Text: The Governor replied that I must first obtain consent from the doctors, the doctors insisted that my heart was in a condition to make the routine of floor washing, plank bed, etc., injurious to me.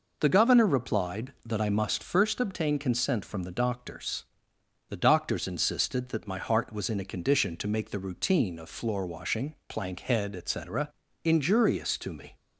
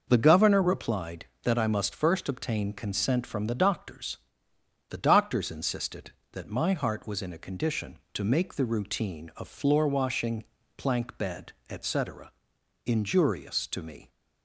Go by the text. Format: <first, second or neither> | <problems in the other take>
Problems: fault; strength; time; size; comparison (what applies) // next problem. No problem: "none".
second | says "head" for "bed"; at 10.0 s